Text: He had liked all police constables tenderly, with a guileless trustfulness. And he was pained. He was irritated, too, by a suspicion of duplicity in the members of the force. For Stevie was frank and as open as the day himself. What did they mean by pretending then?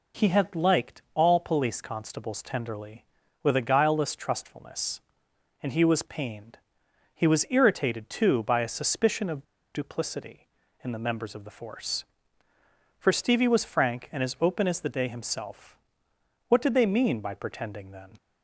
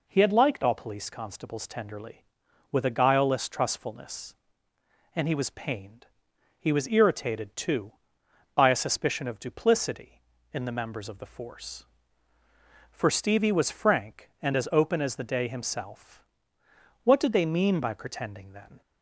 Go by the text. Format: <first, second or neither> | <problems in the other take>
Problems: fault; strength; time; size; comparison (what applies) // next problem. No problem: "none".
second | pauses between "of" and "duplicity"; slight; at 9.4 s; 0.30 s long